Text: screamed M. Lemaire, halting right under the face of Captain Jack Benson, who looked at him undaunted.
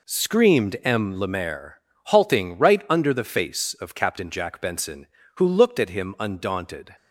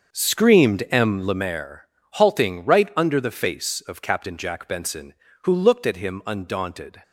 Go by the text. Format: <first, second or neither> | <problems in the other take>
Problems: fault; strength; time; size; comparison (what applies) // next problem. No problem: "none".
first | starts louder than the rest; until 1.5 s; 6.5 dB